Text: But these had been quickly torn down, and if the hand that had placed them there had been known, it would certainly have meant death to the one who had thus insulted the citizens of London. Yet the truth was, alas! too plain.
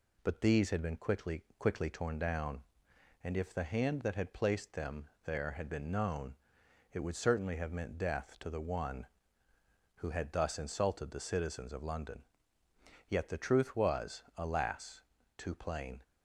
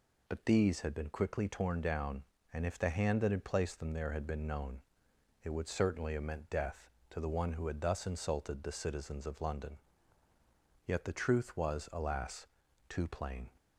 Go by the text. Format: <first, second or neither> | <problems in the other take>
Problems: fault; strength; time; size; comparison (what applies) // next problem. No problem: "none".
second | says "quickly" twice; at 1.5 s // pauses between "them" and "there"; slight; at 5.0 s; 0.18 s long